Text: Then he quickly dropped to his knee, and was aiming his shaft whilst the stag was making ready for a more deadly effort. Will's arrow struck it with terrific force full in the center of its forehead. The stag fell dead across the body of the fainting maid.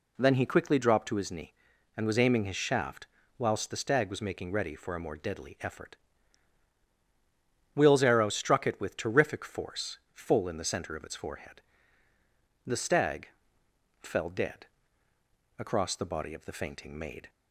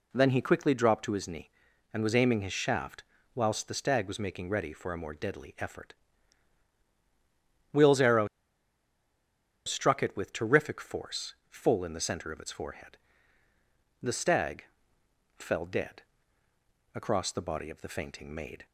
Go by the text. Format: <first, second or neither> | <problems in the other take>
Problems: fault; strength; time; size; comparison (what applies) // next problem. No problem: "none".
first | pauses between "shaft" and "whilst"; slight; at 3.0 s; 0.32 s long; slight in the first // pauses between "arrow" and "struck"; strong; at 8.2 s; 1.3 s long // pauses between "force" and "full"; slight; at 11.3 s; 0.16 s long; slight in the first // pauses between "stag" and "fell"; noticeable; at 14.6 s; 0.74 s long; noticeable in the first // pauses between "dead" and "across"; noticeable; at 16.0 s; 0.92 s long; noticeable in the first